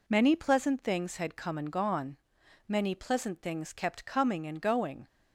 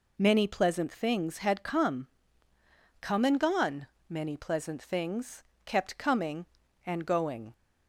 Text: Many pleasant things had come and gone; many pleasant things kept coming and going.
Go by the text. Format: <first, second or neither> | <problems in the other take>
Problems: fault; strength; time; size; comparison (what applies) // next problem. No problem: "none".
first | says "come" twice; at 3.0 s // pauses between "things" and "kept"; slight; at 5.4 s; 0.22 s long